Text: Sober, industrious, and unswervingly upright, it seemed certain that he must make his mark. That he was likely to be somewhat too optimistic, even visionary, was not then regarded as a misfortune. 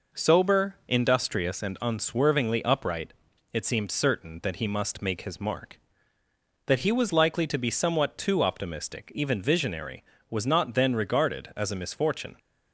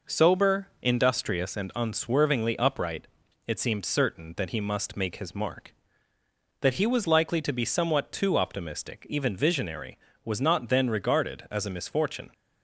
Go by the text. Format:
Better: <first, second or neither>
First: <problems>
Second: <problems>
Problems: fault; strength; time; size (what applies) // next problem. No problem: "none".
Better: neither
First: none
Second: none